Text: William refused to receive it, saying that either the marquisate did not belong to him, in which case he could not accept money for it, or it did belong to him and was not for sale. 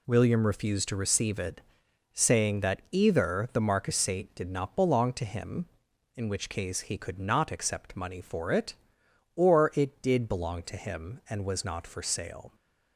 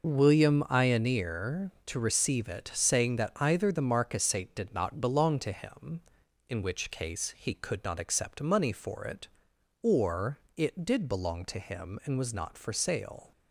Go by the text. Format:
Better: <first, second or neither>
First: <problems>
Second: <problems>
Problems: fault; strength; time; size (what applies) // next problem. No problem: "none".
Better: first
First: none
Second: says "ioneer" for "refused"; at 0.6 s // pauses between "or" and "it"; slight; at 10.3 s; 0.18 s long